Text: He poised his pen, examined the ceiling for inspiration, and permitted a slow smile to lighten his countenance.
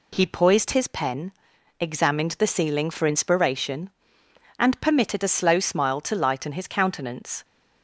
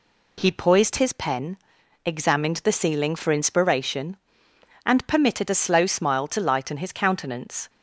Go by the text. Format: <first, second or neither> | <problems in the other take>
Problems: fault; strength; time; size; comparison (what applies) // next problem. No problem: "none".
neither | none